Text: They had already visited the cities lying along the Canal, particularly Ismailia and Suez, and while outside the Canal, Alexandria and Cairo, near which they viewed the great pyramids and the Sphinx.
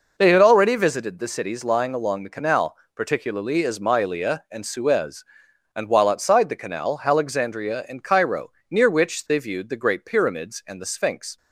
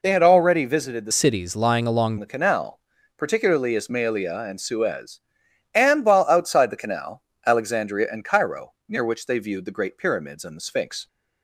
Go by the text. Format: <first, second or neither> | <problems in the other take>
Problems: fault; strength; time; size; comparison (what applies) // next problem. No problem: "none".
first | changes voice from "cities" to "along"; from 1.1 to 2.1 s; 1.0 s long